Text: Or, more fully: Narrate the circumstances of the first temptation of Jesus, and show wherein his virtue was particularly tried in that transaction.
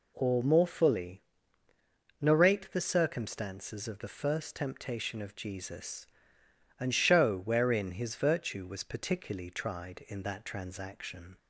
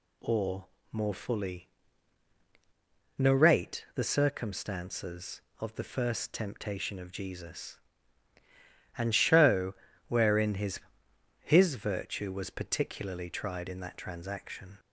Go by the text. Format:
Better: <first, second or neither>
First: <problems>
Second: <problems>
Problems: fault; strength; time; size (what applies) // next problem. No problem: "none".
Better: first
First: none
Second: pauses between "show" and "wherein"; slight; at 9.7 s; 0.32 s long // says "his" twice; at 11.4 s